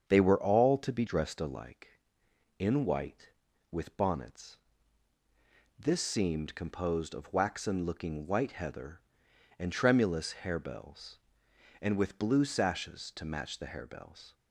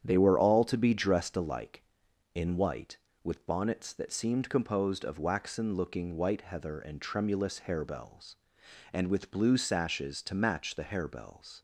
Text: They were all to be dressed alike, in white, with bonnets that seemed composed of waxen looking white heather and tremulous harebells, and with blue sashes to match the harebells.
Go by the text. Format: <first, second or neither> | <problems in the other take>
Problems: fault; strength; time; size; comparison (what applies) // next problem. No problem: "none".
second | starts louder than the rest; strong; until 1.1 s; 7.5 dB; strong in the second // says "this" for "that"; at 5.7 s